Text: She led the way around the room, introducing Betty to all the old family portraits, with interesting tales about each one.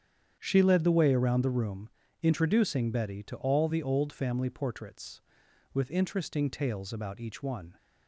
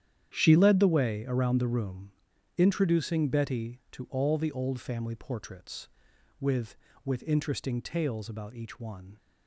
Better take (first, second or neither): first